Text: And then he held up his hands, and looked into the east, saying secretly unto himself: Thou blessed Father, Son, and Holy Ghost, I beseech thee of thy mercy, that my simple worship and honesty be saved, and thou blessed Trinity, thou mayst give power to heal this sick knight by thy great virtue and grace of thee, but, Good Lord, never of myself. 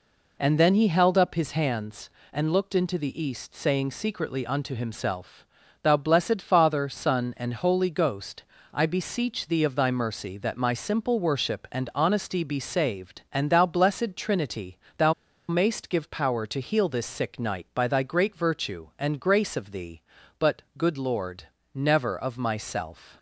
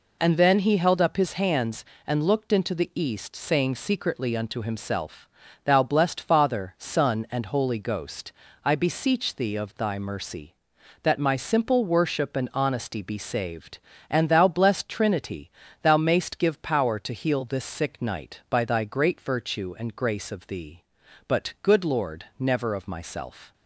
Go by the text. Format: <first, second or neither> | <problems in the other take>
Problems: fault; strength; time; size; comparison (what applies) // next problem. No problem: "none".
second | pauses between "thou" and "mayst"; slight; at 15.1 s; 0.36 s long